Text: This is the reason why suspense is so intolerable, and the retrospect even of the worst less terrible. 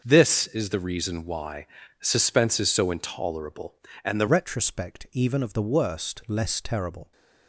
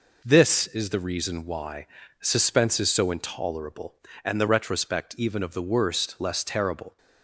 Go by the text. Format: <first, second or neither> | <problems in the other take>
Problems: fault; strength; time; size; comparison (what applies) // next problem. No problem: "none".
second | starts louder than the rest; until 1.0 s; 6.5 dB // pauses between "why" and "suspense"; slight; at 1.6 s; 0.34 s long; slight in the second // changes voice at "retrospect"; from 4.2 s on; 2.9 s long